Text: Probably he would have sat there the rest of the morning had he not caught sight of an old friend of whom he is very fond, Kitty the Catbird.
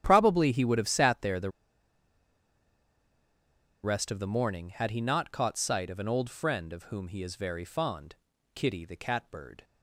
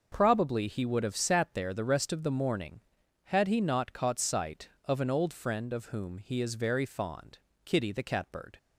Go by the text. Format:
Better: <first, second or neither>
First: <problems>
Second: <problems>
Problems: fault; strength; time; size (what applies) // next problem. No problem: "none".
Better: second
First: starts louder than the rest; strong; until 1.0 s; 10 dB // pauses between "the" and "rest"; strong; at 1.4 s; 2.3 s long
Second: none